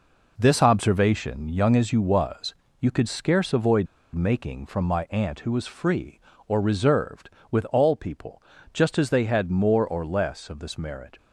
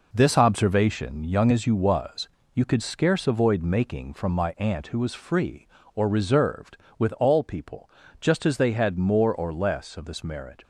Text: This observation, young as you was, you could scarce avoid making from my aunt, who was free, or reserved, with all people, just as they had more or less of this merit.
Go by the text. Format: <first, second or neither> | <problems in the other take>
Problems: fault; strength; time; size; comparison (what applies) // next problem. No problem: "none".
second | pauses between "avoid" and "making"; slight; at 3.8 s; 0.28 s long